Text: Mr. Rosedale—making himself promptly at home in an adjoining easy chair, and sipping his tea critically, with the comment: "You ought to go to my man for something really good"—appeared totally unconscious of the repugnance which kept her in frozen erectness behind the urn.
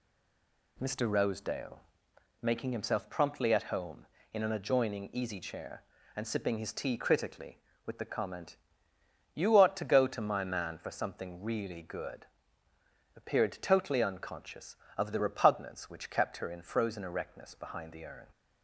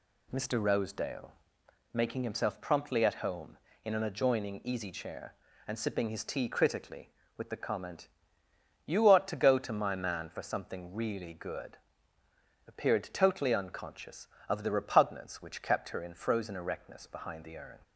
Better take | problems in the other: second | stays silent before the first word; slight; until 0.7 s; 0.7 s long

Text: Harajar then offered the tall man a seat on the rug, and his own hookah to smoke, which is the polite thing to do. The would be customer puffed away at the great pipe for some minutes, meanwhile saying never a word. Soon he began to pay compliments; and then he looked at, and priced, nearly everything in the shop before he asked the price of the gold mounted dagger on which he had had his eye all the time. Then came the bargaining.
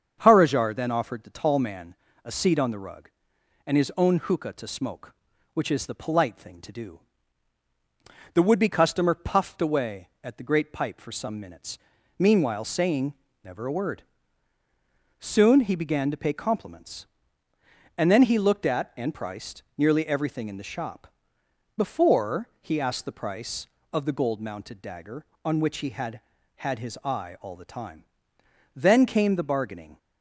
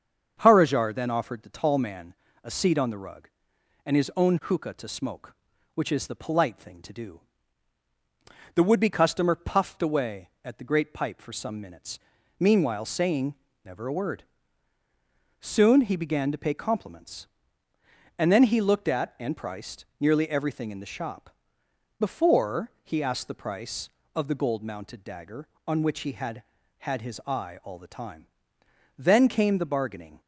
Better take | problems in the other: neither | starts louder than the rest; strong; the same in both // pauses between "man" and "a"; slight; the same in both // pauses between "saying" and "never"; slight; the same in both // pauses between "shop" and "before"; noticeable; the same in both

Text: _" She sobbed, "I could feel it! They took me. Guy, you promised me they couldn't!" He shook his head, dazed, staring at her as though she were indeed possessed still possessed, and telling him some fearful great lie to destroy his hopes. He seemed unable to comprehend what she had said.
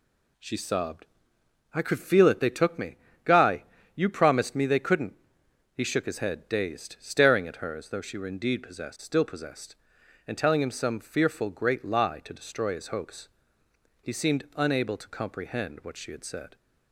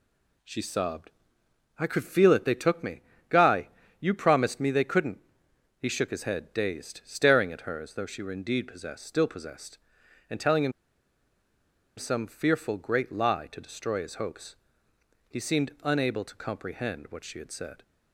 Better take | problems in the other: first | pauses between "him" and "some"; strong; at 10.7 s; 1.2 s long

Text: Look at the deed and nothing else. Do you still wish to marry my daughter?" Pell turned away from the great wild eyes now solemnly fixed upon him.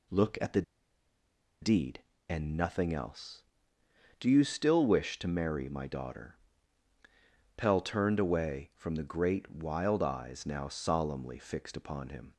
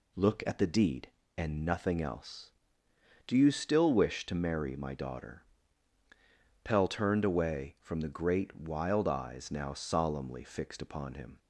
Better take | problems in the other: second | pauses between "the" and "deed"; at 0.6 s; 0.99 s long

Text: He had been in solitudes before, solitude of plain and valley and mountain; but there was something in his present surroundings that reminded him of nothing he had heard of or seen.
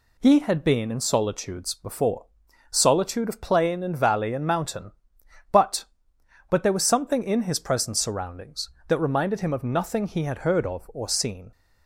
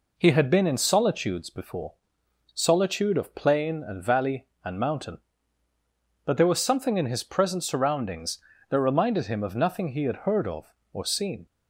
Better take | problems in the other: second | says "but" twice; at 6.4 s

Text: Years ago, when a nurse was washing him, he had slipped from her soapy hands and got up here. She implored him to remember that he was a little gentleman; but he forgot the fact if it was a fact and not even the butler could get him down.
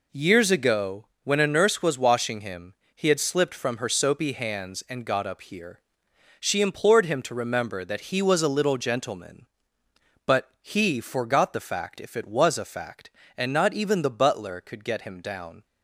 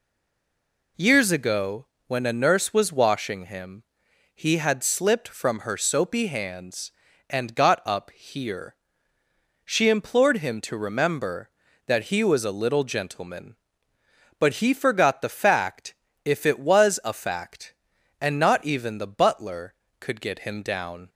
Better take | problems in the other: first | stays silent before the first word; until 0.9 s; 0.9 s long // pauses between "fact" and "if"; slight; at 15.9 s; 0.30 s long

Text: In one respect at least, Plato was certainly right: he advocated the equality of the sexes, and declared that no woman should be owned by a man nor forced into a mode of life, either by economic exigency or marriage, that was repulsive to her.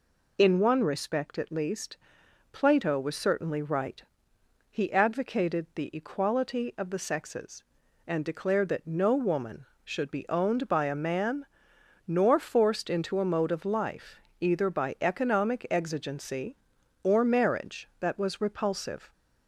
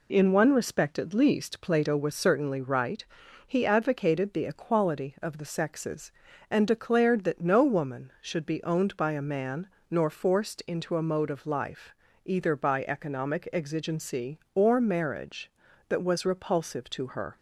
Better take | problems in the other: second | pauses between "man" and "nor"; noticeable; at 11.4 s; 0.62 s long; slight in the second // stops before "to her"; at 19.1 s

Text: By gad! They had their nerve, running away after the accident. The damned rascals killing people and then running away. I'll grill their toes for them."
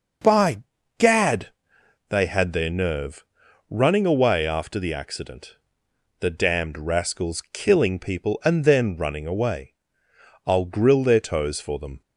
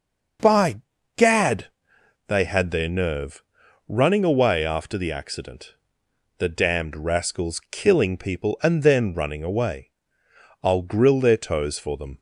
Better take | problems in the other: neither | pauses between "By" and "gad"; slight; the same in both

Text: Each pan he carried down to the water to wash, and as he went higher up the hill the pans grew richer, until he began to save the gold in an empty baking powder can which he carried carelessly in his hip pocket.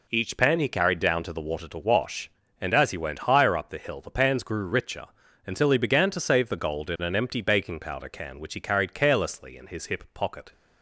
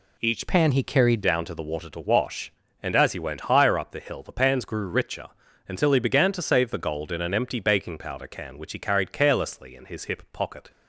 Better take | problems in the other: first | changes voice from "pan" to "carried"; from 0.4 to 1.2 s; 0.8 s long

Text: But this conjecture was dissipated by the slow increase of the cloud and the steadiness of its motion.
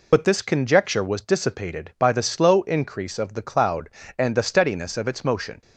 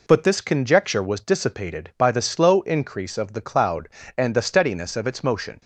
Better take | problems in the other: second | loses the start of "But"; at 0.1 s; 35 ms

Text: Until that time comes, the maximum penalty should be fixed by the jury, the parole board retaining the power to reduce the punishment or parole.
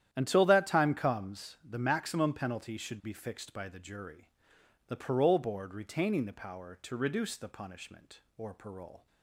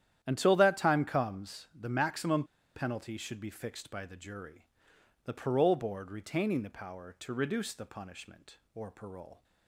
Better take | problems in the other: first | starts louder than the rest; strong; until 1.2 s; 10.5 dB; strong in the first // pauses between "maximum" and "penalty"; slight; at 2.4 s; 0.32 s long

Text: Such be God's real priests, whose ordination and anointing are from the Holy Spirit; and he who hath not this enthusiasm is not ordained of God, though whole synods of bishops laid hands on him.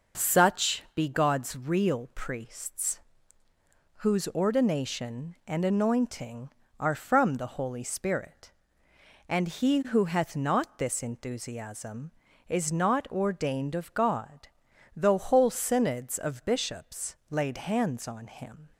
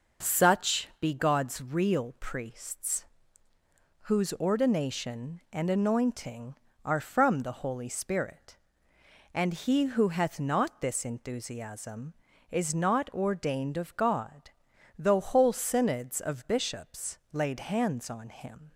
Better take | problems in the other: neither | pauses between "bishops" and "laid"; slight; the same in both

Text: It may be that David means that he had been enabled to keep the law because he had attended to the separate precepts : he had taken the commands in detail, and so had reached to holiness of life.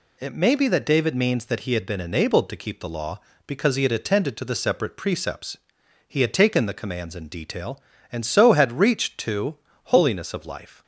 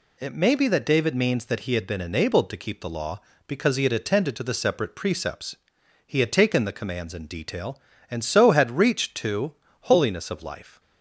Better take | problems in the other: neither | pauses between "to" and "holiness"; slight; the same in both

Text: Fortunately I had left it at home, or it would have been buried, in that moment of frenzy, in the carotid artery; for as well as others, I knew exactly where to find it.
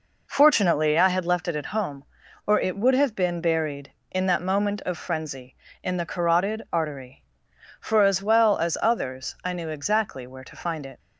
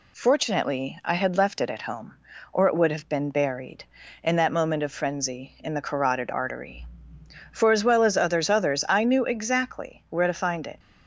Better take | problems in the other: first | says "others" twice; at 8.4 s

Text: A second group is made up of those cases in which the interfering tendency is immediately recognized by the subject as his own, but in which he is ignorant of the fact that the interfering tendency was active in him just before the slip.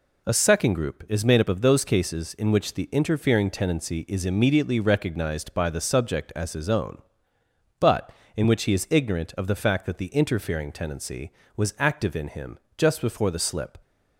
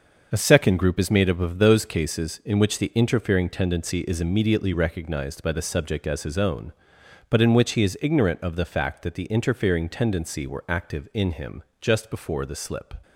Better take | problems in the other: first | starts louder than the rest; until 1.3 s; 6.5 dB // says "were" for "was"; at 10.4 s // pauses between "him" and "just"; slight; at 11.6 s; 0.20 s long; slight in the first

